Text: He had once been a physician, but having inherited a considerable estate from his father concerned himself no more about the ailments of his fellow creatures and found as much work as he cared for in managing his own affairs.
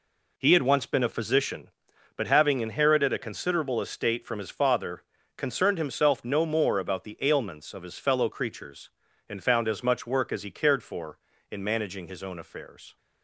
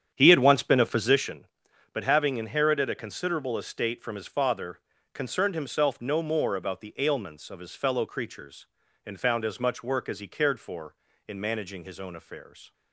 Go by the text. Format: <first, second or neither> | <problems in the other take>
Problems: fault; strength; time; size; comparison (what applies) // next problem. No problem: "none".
first | starts louder than the rest; strong; until 1.4 s; 9 dB // pauses between "father" and "concerned"; slight; at 4.7 s; 0.34 s long; slight in the first